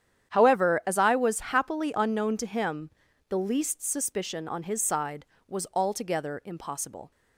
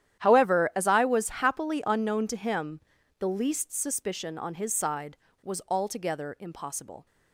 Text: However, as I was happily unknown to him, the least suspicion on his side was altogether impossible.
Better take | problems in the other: first | gets quieter; strong; throughout; 16.5 dB // starts louder than the rest; strong; until 1.2 s; 10.5 dB; strong in the first

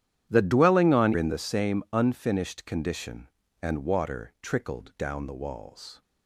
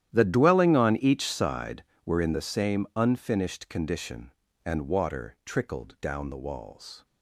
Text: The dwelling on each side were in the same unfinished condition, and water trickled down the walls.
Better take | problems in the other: second | starts louder than the rest; strong; until 1.3 s; 11 dB; strong in the second // skips "each side were"; at 1.1 s

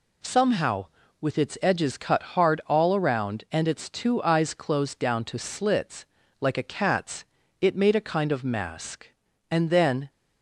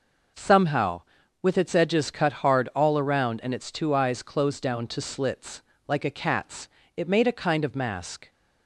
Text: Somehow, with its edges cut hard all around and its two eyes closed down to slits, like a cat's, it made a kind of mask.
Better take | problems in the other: second | pauses between "cut" and "hard"; slight; at 2.2 s; 0.16 s long // goes on to say "And then"; from 9.4 s on; 0.60 s long

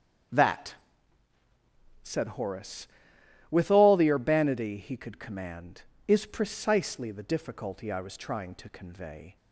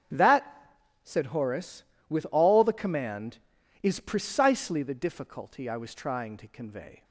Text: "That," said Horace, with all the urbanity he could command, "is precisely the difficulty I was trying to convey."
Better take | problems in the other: first | starts louder than the rest; strong; until 1.4 s; 7.5 dB; also in the first // skips "urbanity he could"; at 2.7 s

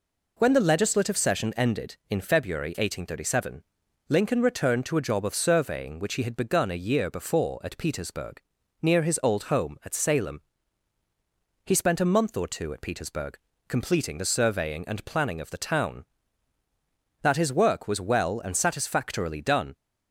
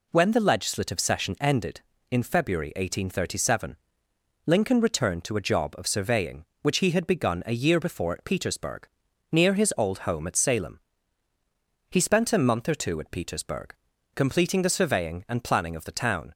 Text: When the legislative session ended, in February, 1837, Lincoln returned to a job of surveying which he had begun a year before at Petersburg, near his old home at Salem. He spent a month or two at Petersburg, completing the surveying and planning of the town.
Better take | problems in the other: second | goes on to say "That his work was well and satisfactorily done"; strong; from 17.2 s on; 2.5 s long

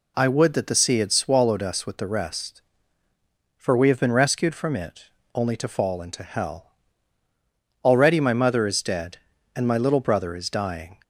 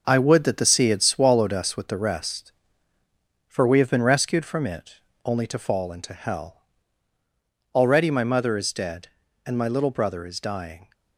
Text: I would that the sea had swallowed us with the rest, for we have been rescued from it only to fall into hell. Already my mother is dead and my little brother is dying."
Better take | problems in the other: first | gets quieter; strong; throughout; 7 dB // pauses between "it" and "only"; slight; at 5.0 s; 0.24 s long; slight in the first

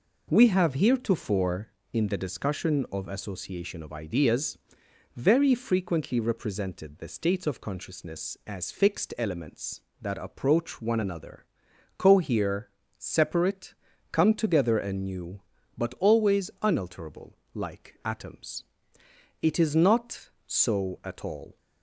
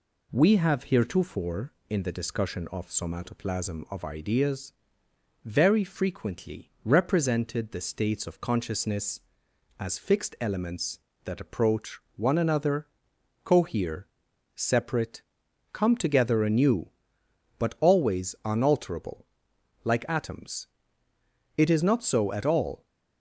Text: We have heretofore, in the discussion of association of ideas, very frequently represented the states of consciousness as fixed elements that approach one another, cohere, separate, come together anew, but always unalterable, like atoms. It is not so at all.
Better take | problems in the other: first | says "somatoplasm" for "association"; at 2.8 s // pauses between "approach" and "one"; slight; at 11.9 s; 0.18 s long

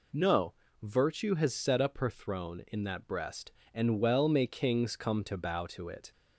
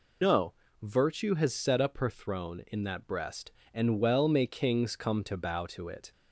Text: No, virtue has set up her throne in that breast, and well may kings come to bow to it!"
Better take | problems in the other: first | loses the start of "No"; at 0.2 s; 90 ms

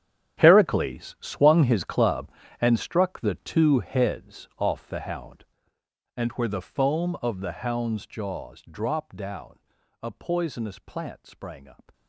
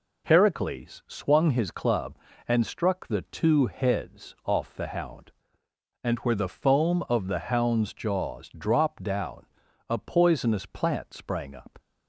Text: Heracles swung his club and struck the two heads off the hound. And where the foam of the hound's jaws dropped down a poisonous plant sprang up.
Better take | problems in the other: second | gets quieter; strong; throughout; 15.5 dB // pauses between "down" and "a"; at 9.5 s; 0.42 s long; also in the second

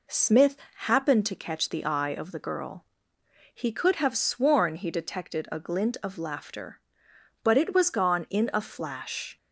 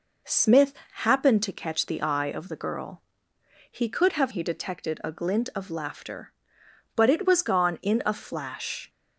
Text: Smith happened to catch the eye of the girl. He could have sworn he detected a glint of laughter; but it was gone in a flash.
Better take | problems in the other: first | pauses between "Smith" and "happened"; slight; at 0.7 s; 0.32 s long; slight in the first // skips "sworn"; at 4.3 s

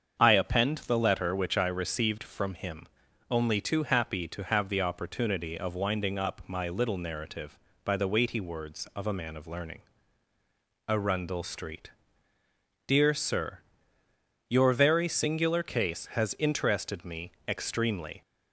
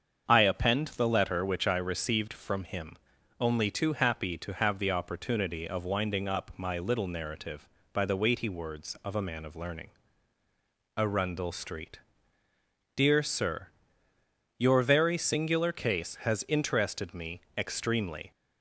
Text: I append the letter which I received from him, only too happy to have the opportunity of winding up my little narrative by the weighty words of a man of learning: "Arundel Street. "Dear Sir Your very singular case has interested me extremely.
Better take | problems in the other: neither | starts louder than the rest; the same in both // pauses between "Sir" and "Your"; noticeable; the same in both // pauses between "me" and "extremely"; slight; the same in both

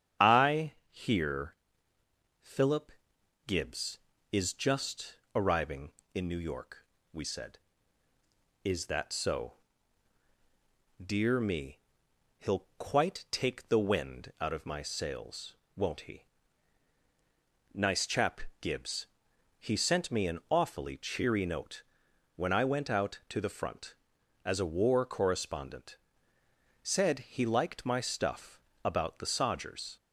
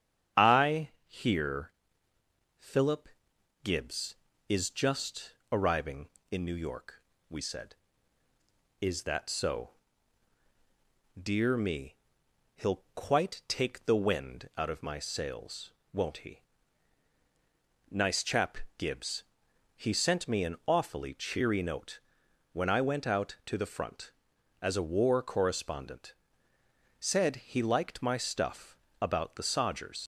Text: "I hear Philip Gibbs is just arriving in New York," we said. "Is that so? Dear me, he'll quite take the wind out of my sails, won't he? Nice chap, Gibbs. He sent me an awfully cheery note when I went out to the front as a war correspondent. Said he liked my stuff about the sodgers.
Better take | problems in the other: first | starts louder than the rest; strong; until 1.5 s; 8 dB; strong in the first // pauses between "I" and "hear"; slight; at 0.8 s; 0.18 s long; slight in the first // pauses between "hear" and "Philip"; noticeable; at 1.7 s; 0.88 s long; noticeable in the first // pauses between "Philip" and "Gibbs"; noticeable; at 3.0 s; 0.56 s long; noticeable in the first // pauses between "just" and "arriving"; slight; at 5.3 s; 0.16 s long; slight in the first // pauses between "note" and "when"; noticeable; at 22.0 s; 0.50 s long; noticeable in the first // pauses between "stuff" and "about"; slight; at 28.7 s; 0.24 s long; slight in the first // leaves "sodgers" unfinished; at 30.0 s; 70 ms

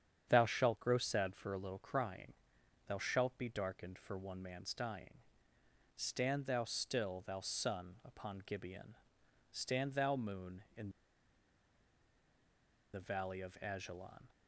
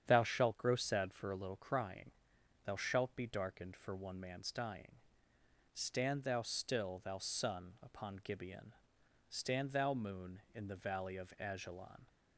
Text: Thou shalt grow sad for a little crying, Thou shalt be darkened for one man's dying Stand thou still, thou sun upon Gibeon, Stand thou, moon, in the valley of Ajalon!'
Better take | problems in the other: second | starts louder than the rest; strong; until 1.3 s; 8.5 dB; strong in the second // pauses between "dying" and "Stand"; noticeable; at 5.1 s; 0.78 s long; noticeable in the second // pauses between "in" and "the"; strong; at 10.8 s; 2.0 s long

